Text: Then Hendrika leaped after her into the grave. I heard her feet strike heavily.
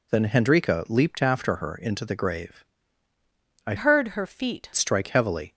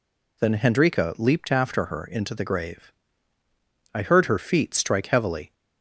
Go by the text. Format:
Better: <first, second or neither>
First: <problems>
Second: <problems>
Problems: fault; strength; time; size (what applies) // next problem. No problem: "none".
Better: second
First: changes voice from "heard" to "feet"; from 3.7 to 4.6 s; 0.9 s long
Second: none